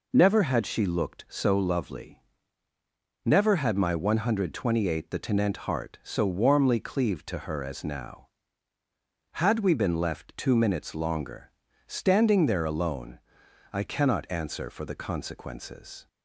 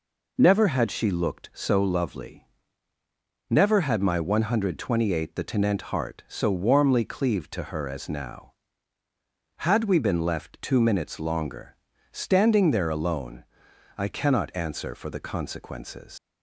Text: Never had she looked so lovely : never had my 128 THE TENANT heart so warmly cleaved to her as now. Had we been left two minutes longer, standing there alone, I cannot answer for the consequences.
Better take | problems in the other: first | leaves "consequences" unfinished; at 16.1 s; 140 ms

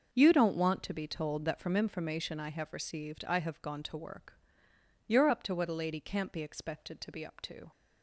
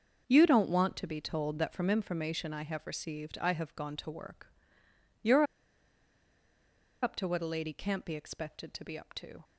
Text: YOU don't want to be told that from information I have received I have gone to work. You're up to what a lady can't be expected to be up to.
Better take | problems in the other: first | starts louder than the rest; until 1.2 s; 6.5 dB; also in the first // pauses between "You're" and "up"; strong; at 5.4 s; 1.5 s long

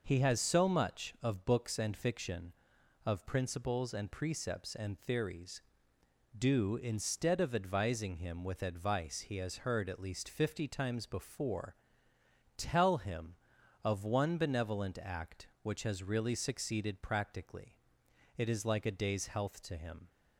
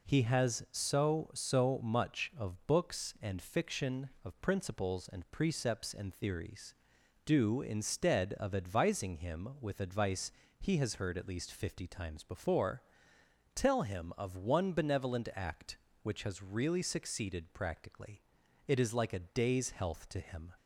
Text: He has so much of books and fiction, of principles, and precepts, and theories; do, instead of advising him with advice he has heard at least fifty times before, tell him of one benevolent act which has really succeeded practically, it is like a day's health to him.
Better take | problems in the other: first | says "so" twice; at 1.3 s // pauses between "advice" and "he"; slight; at 10.3 s; 0.28 s long

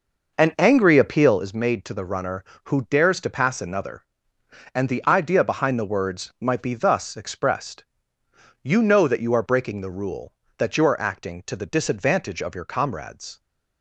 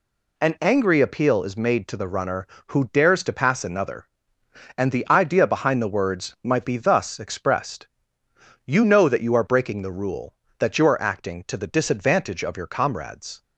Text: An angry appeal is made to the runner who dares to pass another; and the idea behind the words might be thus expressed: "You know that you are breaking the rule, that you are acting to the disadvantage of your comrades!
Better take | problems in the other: second | starts louder than the rest; noticeable; until 1.5 s; 5.5 dB

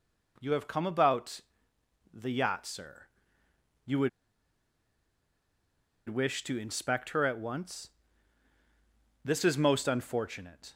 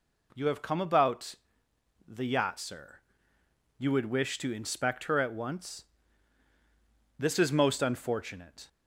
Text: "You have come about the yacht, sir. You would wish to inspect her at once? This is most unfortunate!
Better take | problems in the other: second | pauses between "about" and "the"; noticeable; at 1.4 s; 0.72 s long; noticeable in the second // pauses between "would" and "wish"; strong; at 4.0 s; 1.9 s long

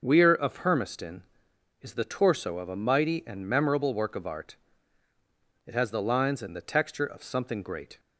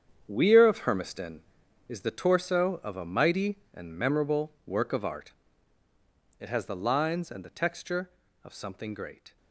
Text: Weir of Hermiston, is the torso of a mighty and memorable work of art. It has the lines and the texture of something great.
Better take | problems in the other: first | gets quieter; strong; throughout; 12.5 dB // starts louder than the rest; strong; until 1.2 s; 8 dB; noticeable in the first

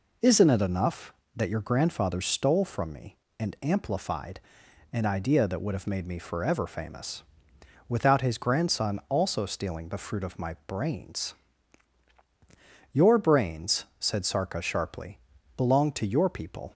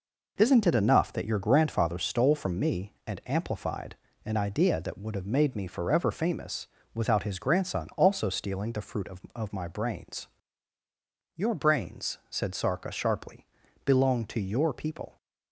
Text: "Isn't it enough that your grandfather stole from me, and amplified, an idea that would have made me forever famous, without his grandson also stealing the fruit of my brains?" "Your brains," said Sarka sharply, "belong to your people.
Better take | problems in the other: first | says "of" twice; at 9.3 s

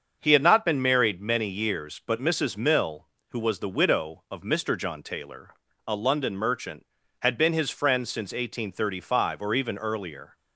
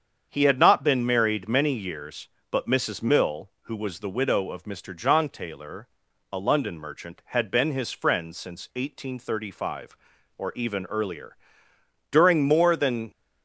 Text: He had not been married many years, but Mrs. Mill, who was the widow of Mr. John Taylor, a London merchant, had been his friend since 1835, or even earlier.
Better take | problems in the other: first | starts louder than the rest; strong; until 1.3 s; 7.5 dB; also in the first // goes on to say "During more than"; noticeable; from 12.1 s on; 0.98 s long

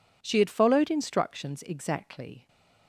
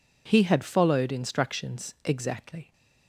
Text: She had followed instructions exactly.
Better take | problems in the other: first | says "He" for "She"; at 0.2 s

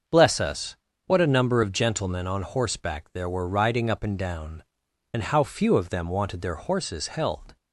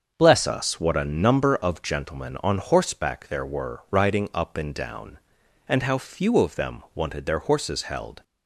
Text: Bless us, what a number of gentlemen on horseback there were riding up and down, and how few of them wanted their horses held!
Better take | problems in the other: first | starts louder than the rest; until 1.1 s; 6.5 dB; also in the first // changes voice at "us"; from 0.4 s on; 7.8 s long

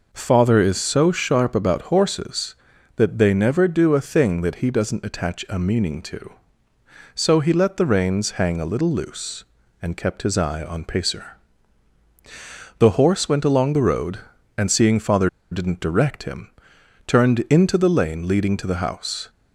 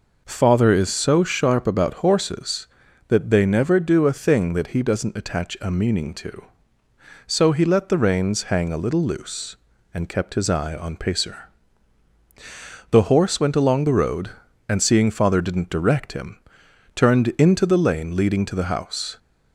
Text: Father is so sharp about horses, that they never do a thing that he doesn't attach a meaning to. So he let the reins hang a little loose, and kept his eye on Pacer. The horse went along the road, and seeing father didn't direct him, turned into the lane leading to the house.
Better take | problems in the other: second | pauses between "father" and "didn't"; slight; at 15.2 s; 0.22 s long

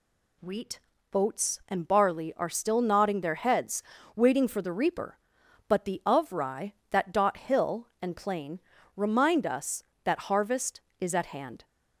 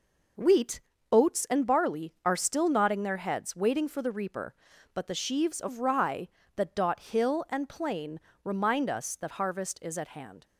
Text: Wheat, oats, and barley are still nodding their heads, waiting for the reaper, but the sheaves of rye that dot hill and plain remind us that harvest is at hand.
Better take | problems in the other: second | skips "sheaves"; at 6.0 s // pauses between "plain" and "remind"; slight; at 8.6 s; 0.34 s long; slight in the second

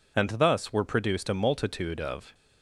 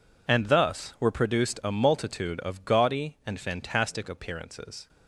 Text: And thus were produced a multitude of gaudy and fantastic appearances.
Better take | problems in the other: second | stops before "gaudy and fantastic appearances"; at 2.3 s

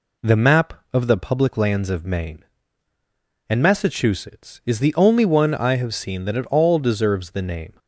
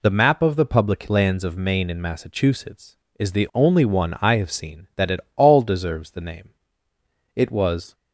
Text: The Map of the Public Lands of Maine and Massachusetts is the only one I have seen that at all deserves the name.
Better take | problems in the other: first | pauses between "at" and "all"; slight; at 5.2 s; 0.16 s long // goes on to say "It was"; from 7.3 s on; 0.58 s long

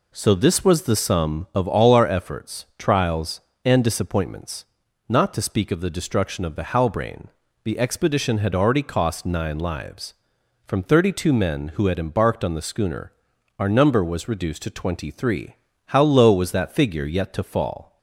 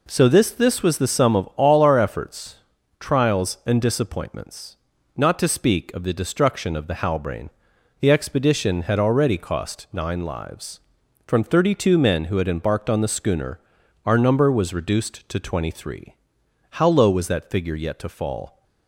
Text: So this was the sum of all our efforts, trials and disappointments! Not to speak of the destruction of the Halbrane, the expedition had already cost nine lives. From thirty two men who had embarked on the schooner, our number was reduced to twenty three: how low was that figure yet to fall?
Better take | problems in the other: first | says "this" twice; at 0.5 s

